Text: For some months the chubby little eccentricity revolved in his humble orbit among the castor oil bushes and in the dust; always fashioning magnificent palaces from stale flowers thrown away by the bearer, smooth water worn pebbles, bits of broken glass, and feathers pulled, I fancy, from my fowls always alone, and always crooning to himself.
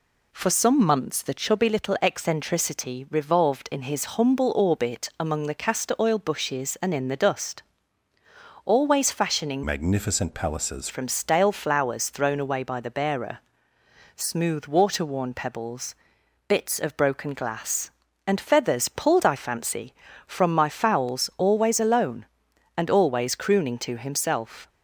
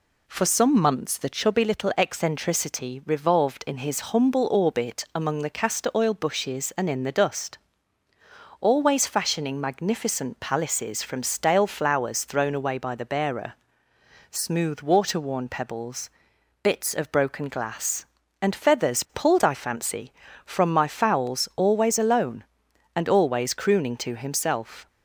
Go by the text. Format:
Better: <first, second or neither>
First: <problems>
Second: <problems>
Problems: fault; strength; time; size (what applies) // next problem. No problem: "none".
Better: second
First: changes voice from "magnificent" to "palaces"; from 9.6 to 10.8 s; 1.2 s long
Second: none